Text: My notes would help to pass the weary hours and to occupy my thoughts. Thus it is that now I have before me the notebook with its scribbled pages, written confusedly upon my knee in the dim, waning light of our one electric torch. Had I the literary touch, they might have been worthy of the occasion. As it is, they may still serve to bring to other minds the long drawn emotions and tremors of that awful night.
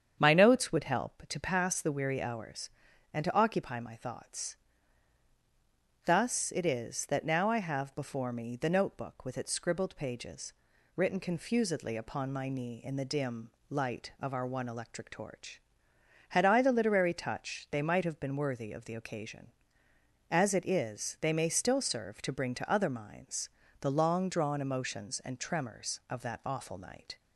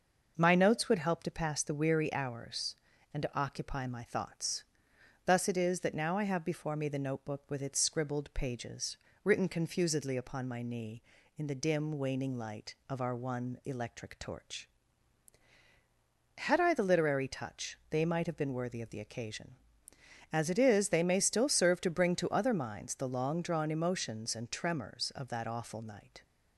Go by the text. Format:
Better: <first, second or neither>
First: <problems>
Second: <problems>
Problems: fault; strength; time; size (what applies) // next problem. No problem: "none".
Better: second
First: starts louder than the rest; strong; until 1.2 s; 8 dB // skips "waning"; at 13.5 s // pauses between "minds" and "the"; slight; at 23.4 s; 0.32 s long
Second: starts louder than the rest; noticeable; until 1.3 s; 6 dB